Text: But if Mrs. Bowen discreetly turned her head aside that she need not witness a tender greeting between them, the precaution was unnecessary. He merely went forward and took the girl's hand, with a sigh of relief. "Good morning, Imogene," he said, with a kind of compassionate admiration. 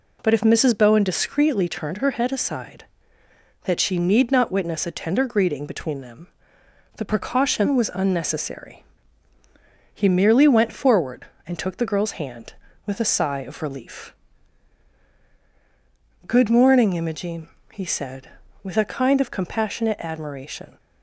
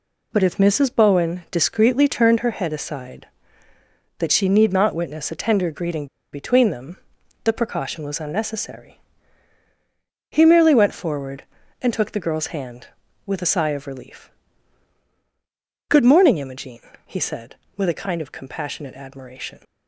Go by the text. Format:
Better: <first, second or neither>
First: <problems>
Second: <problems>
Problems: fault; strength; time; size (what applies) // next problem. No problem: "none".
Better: first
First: none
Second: pauses between "greeting" and "between"; slight; at 6.0 s; 0.25 s long